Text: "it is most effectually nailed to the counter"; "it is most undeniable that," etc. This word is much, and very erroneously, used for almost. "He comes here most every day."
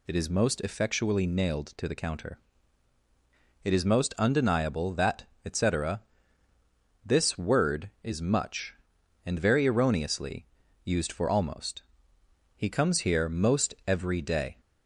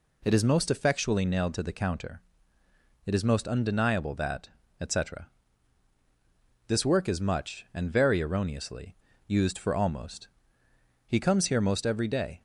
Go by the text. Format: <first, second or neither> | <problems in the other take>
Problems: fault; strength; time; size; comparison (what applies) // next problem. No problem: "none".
first | says "work" for "word"; at 6.8 s